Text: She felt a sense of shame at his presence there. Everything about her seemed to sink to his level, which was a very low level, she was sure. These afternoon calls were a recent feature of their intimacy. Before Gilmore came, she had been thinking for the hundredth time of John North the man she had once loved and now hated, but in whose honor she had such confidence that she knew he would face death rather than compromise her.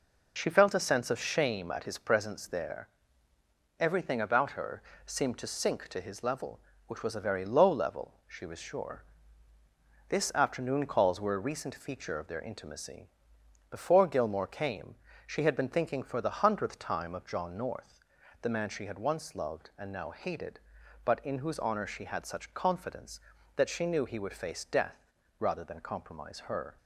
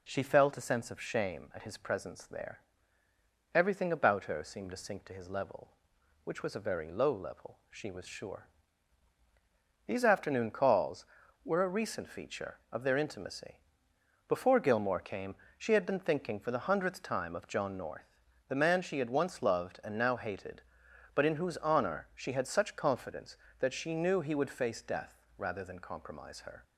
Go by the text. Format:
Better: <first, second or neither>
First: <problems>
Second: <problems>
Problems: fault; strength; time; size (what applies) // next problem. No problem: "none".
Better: second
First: pauses between "her" and "seemed"; slight; at 4.8 s; 0.24 s long // says "This" for "These"; at 10.0 s // pauses between "North" and "the"; at 18.0 s; 0.40 s long // pauses between "death" and "rather"; slight; at 25.0 s; 0.32 s long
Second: pauses between "North" and "the"; slight; at 18.1 s; 0.32 s long // pauses between "death" and "rather"; slight; at 25.1 s; 0.18 s long